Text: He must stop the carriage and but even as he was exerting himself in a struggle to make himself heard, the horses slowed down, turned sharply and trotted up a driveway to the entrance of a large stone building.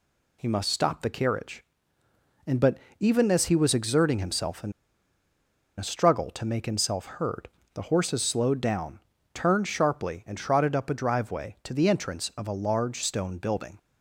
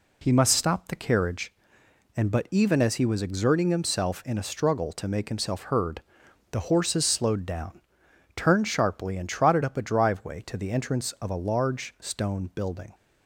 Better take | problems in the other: second | pauses between "but" and "even"; slight; at 2.7 s; 0.20 s long // pauses between "in" and "a"; at 4.7 s; 1.0 s long

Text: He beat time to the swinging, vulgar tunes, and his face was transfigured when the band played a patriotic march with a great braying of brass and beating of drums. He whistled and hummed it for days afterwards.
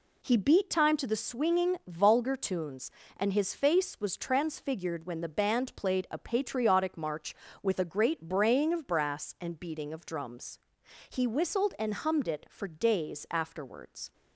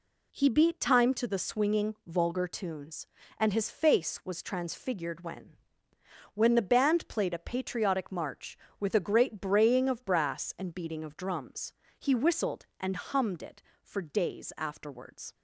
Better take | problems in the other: first | says "when" twice; at 6.3 s

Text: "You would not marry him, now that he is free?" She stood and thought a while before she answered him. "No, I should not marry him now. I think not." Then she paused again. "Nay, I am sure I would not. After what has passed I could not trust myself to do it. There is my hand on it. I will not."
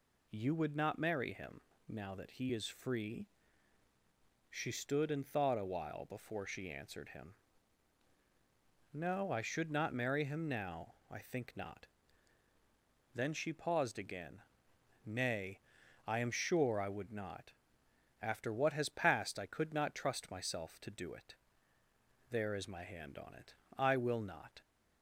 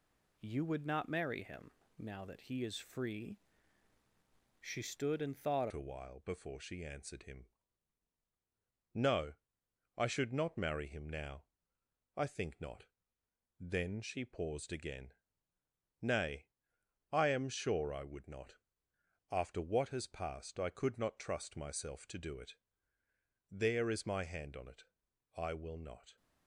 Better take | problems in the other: first | changes voice at "a"; from 5.7 s on; 20.4 s long

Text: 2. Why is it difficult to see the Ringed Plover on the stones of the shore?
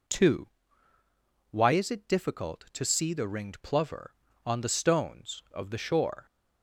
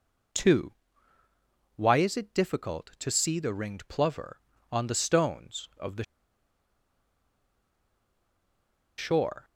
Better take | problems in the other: first | pauses between "the" and "shore"; strong; at 6.0 s; 2.9 s long

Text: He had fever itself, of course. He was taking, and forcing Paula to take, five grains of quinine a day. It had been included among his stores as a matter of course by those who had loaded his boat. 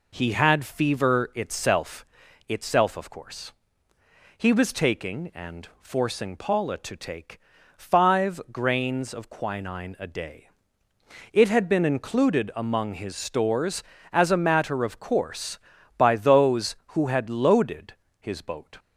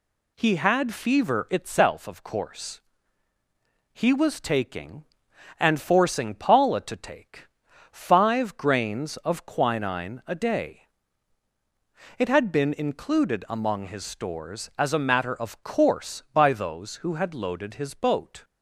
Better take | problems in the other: second | says "itself" twice; at 2.4 s // pauses between "loaded" and "his"; slight; at 17.9 s; 0.26 s long

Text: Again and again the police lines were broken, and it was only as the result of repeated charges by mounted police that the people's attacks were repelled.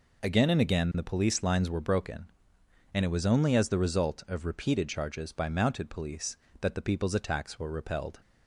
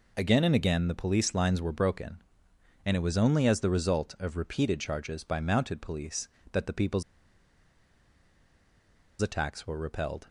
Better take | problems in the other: first | pauses between "people's" and "attacks"; strong; at 7.0 s; 2.1 s long

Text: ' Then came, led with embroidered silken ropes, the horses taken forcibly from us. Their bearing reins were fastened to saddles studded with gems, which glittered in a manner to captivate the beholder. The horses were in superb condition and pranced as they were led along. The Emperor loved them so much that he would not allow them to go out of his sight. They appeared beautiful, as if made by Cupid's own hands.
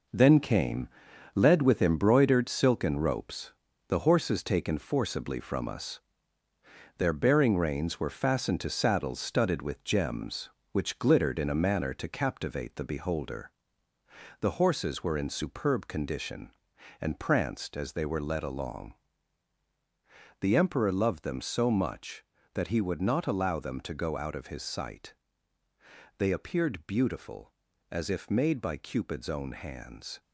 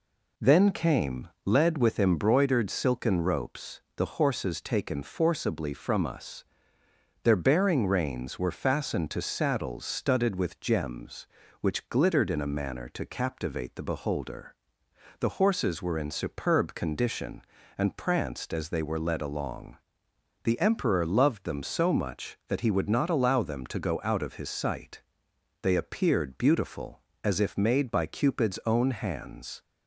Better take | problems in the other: second | gets quieter; strong; throughout; 7.5 dB

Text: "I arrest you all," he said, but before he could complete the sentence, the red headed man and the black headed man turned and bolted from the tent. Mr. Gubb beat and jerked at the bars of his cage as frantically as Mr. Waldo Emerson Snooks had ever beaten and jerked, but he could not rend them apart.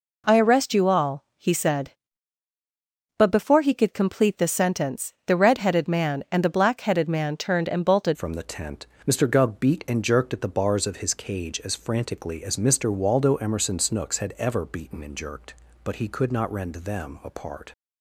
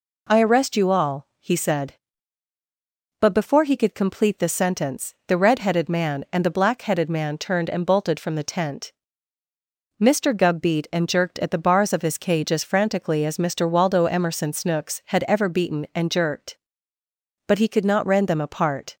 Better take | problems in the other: second | changes voice at "from"; from 8.1 s on; 9.6 s long

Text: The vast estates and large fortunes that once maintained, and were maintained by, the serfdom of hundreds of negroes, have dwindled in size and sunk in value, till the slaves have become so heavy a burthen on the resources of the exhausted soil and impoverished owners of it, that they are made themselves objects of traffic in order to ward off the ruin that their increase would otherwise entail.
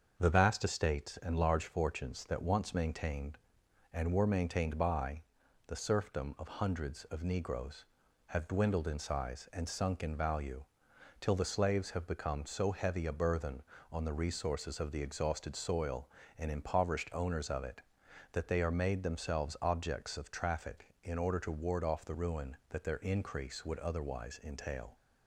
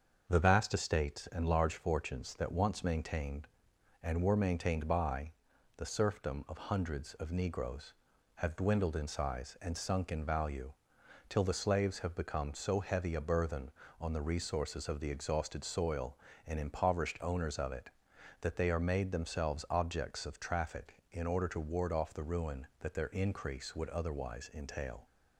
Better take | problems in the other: neither | starts louder than the rest; the same in both

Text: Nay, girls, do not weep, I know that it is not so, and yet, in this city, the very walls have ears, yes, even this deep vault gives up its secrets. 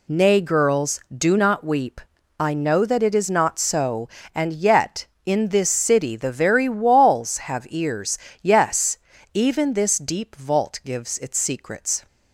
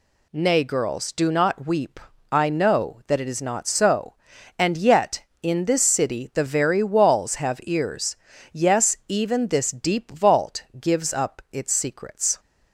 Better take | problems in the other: second | skips "up"; at 11.1 s

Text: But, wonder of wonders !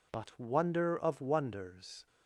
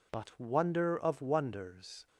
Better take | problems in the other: neither | none

